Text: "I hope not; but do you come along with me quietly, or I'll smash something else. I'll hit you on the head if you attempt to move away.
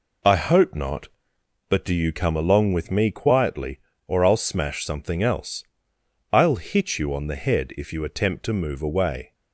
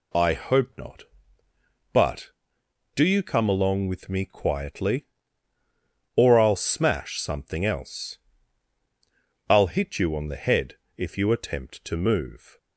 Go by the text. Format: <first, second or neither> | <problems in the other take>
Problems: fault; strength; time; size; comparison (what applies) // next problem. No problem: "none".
first | pauses between "head" and "if"; slight; at 10.7 s; 0.22 s long // stops before "away"; at 12.5 s